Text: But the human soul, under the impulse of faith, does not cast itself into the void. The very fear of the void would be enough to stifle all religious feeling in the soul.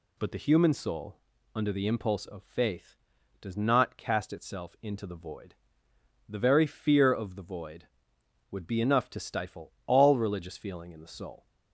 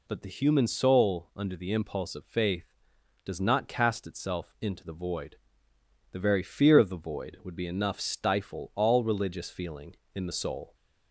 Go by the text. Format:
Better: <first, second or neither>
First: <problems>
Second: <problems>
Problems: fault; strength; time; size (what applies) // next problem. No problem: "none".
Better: first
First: none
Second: skips "to"; at 7.9 s